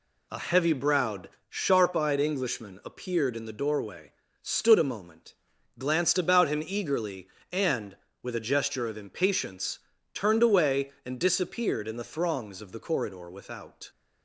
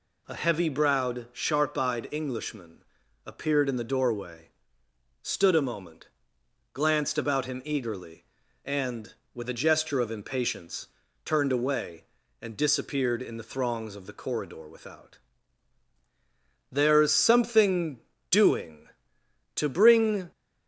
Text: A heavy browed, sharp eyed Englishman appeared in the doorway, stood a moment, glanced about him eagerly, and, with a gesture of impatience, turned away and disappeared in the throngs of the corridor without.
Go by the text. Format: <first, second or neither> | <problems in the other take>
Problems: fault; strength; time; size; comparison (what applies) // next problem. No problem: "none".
first | pauses between "Englishman" and "appeared"; at 2.8 s; 0.44 s long // goes on to say "There's something doing to bring"; strong; from 16.7 s on; 3.6 s long